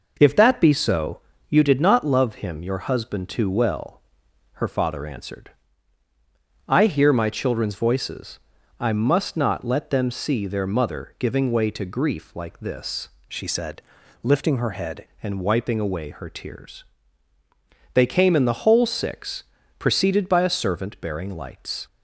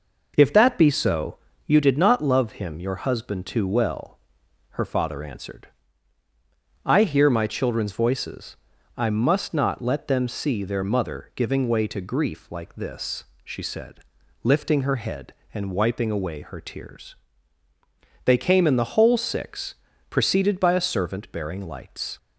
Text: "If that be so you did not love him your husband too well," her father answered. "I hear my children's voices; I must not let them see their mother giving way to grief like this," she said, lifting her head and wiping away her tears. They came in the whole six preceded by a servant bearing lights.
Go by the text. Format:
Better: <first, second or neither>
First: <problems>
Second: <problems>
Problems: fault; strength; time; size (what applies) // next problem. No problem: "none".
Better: second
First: pauses between "so" and "you"; slight; at 1.1 s; 0.30 s long // changes voice from "she" to "head"; from 13.2 to 15.0 s; 1.8 s long // pauses between "six" and "preceded"; slight; at 19.4 s; 0.34 s long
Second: pauses between "so" and "you"; slight; at 1.3 s; 0.30 s long // pauses between "six" and "preceded"; slight; at 19.7 s; 0.34 s long